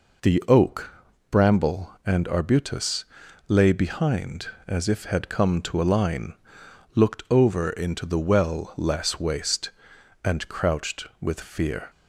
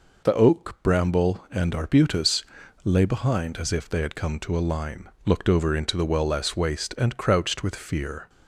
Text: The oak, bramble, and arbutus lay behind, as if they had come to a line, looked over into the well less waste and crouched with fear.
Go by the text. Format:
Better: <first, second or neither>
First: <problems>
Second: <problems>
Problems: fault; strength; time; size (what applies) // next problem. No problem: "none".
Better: second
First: pauses between "arbutus" and "lay"; at 3.0 s; 0.44 s long // skips "they"; at 5.0 s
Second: pauses between "arbutus" and "lay"; at 2.4 s; 0.40 s long